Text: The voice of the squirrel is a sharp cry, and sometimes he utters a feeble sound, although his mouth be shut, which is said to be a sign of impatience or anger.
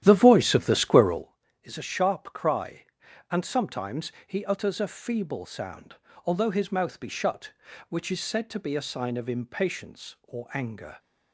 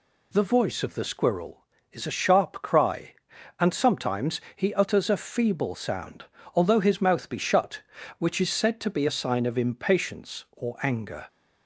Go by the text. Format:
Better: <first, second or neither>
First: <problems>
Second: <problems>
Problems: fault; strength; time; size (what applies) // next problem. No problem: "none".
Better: second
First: starts louder than the rest; strong; until 1.3 s; 11.5 dB // pauses between "sometimes" and "he"; slight; at 4.1 s; 0.16 s long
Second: pauses between "sometimes" and "he"; slight; at 4.4 s; 0.16 s long